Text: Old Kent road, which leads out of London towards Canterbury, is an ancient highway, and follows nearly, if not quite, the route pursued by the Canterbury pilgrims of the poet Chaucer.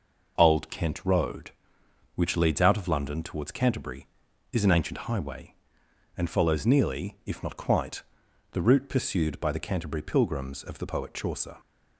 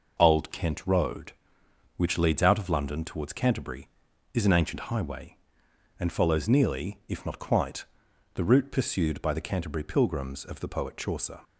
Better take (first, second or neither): neither